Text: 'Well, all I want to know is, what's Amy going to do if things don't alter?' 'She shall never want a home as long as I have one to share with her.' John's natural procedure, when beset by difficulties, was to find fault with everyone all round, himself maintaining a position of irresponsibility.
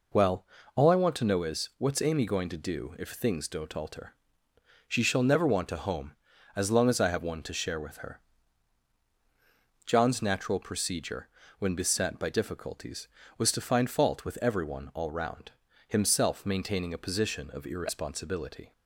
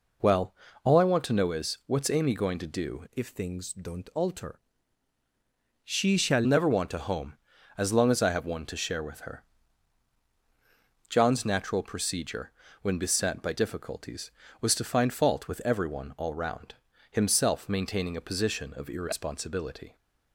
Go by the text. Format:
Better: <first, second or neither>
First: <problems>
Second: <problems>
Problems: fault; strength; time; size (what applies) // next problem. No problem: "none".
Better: first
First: none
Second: changes voice from "if" to "shall"; from 3.1 to 6.4 s; 3.3 s long